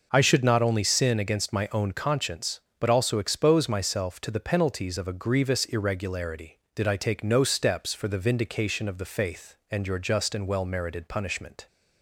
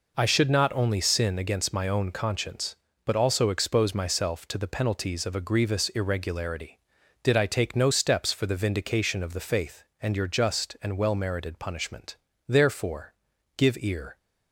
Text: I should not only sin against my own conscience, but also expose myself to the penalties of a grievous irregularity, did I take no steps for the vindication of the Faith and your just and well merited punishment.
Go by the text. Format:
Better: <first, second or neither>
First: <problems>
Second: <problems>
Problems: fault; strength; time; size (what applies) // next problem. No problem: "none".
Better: first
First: none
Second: goes on to say "Therefore give ear"; strong; from 12.4 s on; 1.7 s long